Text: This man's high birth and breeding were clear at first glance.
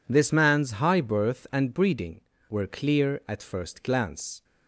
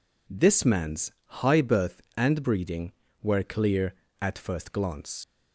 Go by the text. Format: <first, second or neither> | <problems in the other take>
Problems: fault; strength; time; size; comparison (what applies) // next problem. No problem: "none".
first | pauses between "man's" and "high"; slight; at 1.1 s; 0.28 s long // leaves "glance" unfinished; at 5.2 s; 105 ms